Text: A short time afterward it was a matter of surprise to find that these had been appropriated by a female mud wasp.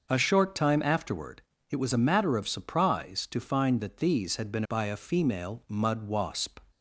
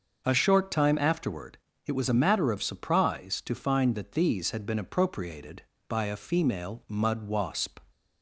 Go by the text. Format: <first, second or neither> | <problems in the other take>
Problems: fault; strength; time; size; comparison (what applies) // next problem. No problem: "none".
second | starts louder than the rest; noticeable; until 1.1 s; 6 dB; also in the second // pauses between "afterward" and "it"; slight; at 1.4 s; 0.28 s long; slight in the second // skips "appropriated"; at 4.6 s